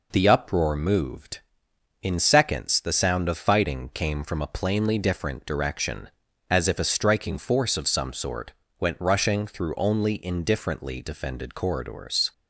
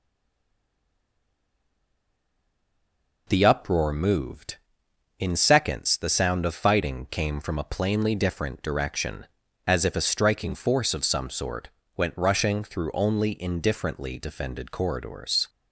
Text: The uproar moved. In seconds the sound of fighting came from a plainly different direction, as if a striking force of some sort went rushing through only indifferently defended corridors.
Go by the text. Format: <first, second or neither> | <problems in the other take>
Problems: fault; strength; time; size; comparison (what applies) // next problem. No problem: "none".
first | stays silent before the first word; strong; until 3.2 s; 3.2 s long // pauses between "sort" and "went"; slight; at 11.6 s; 0.30 s long; slight in the first